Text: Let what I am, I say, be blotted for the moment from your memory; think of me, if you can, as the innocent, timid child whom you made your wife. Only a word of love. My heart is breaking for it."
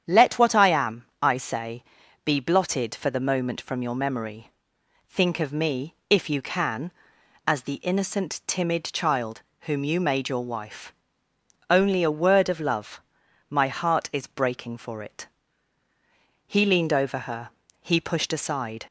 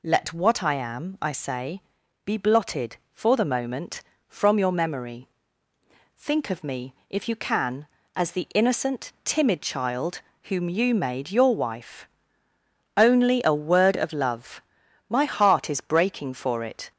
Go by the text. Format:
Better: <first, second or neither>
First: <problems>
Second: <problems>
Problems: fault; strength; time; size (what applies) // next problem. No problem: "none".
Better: second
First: starts louder than the rest; strong; until 1.2 s; 8.5 dB // pauses between "child" and "whom"; slight; at 9.4 s; 0.20 s long // goes on to say "He leaned over her he pushed aside"; strong; from 16.4 s on; 2.3 s long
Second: pauses between "child" and "whom"; slight; at 10.2 s; 0.22 s long